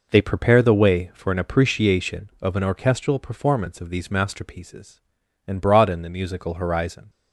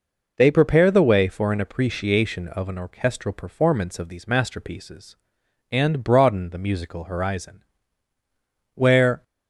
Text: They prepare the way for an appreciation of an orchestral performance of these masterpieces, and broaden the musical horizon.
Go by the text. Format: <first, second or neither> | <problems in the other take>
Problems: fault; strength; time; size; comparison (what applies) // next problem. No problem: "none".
first | goes on to say "Where"; slight; from 8.7 s on; 0.48 s long